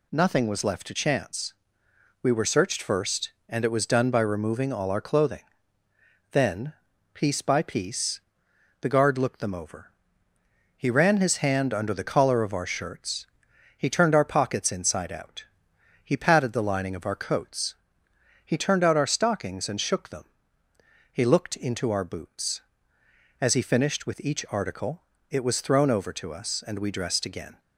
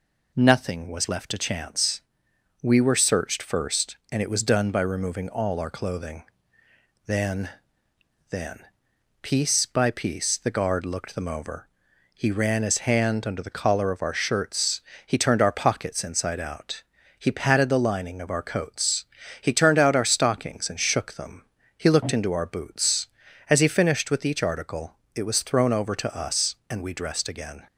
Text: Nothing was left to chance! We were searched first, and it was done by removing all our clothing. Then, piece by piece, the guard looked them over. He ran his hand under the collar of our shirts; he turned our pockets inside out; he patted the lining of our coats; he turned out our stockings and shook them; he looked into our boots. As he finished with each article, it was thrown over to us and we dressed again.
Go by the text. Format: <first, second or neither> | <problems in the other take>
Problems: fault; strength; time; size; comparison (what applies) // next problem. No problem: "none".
first | says "Then" twice; at 8.3 s